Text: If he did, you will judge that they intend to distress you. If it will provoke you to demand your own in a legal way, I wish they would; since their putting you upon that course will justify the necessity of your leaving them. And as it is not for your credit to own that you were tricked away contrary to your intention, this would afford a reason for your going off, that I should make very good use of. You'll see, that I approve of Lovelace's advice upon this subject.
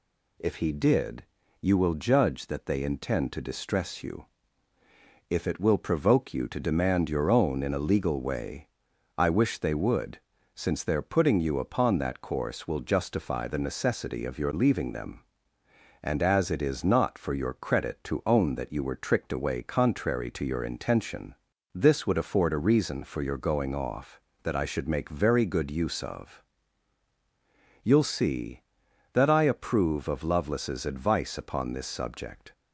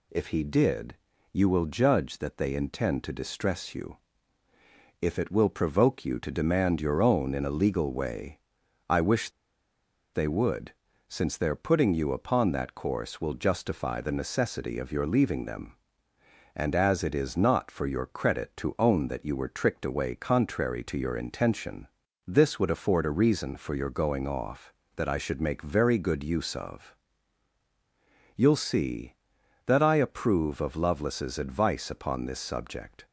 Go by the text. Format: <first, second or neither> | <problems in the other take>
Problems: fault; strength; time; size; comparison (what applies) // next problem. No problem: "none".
first | pauses between "wish" and "they"; noticeable; at 9.2 s; 0.85 s long